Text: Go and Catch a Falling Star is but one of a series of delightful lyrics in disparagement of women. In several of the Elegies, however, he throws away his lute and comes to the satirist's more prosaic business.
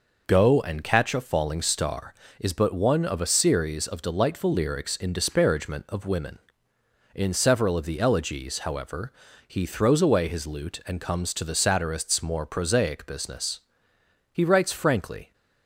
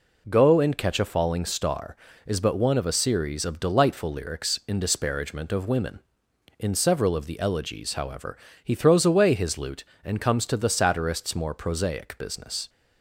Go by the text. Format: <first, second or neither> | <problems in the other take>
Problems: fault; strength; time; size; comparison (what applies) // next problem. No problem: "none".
second | goes on to say "He writes frankly"; noticeable; from 14.3 s on; 1.0 s long